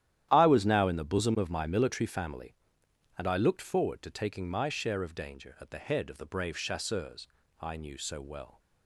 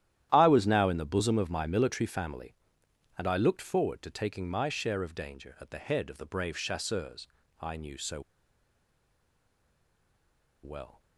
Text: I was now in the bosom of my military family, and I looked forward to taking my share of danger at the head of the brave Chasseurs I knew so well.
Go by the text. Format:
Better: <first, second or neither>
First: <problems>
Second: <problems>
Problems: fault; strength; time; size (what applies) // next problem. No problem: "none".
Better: first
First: starts louder than the rest; strong; until 1.3 s; 11.5 dB // pauses between "Chasseurs" and "I"; slight; at 7.2 s; 0.32 s long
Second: starts louder than the rest; strong; until 1.3 s; 11.5 dB // pauses between "Chasseurs" and "I"; slight; at 7.2 s; 0.32 s long // pauses between "so" and "well"; strong; at 8.2 s; 2.4 s long